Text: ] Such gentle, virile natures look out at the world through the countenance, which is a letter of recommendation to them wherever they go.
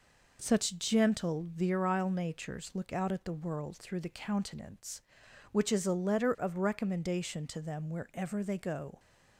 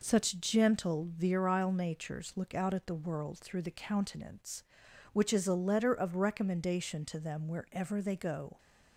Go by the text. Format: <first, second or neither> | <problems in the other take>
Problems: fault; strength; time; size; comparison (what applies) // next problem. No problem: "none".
neither | none